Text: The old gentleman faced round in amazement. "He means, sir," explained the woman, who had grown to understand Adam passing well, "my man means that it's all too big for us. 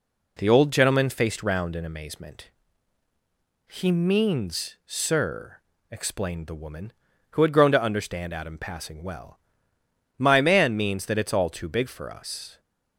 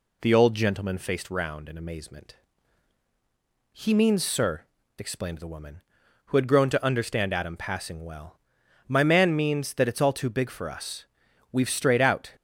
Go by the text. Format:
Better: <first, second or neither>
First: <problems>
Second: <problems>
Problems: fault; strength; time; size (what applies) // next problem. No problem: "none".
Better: first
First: none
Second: goes on to say "We've strayed out"; noticeable; from 11.5 s on; 0.80 s long